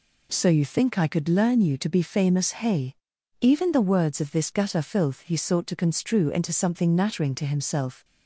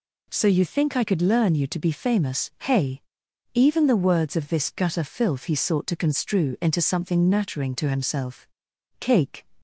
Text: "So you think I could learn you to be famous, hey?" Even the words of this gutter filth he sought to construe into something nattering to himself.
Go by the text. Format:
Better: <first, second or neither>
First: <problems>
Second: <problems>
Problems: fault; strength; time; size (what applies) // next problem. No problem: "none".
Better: first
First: none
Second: goes on to say "Cake"; slight; from 8.9 s on; 0.46 s long